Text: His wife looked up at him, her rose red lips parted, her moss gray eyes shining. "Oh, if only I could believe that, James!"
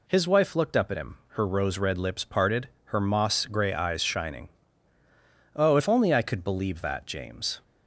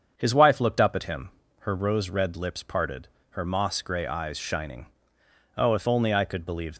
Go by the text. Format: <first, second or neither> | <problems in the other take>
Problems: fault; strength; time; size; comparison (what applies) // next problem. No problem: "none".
first | starts louder than the rest; until 1.1 s; 7 dB // stops before "that James"; at 6.7 s